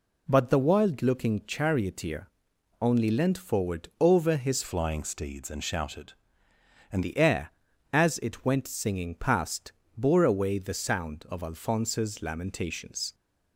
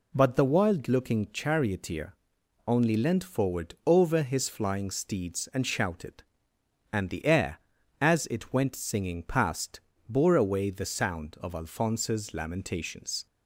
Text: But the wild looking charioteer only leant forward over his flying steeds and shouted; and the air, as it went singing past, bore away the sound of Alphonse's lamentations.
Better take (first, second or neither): second